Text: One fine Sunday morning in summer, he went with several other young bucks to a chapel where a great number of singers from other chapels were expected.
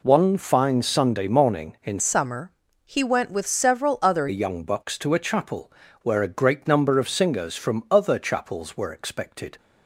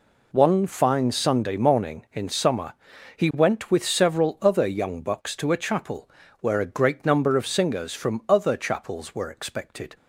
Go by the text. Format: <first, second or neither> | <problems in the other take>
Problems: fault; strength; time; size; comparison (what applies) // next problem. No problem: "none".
second | changes voice from "summer" to "other"; from 1.9 to 4.2 s; 2.3 s long // pauses between "chapel" and "where"; slight; at 5.7 s; 0.32 s long; slight in the second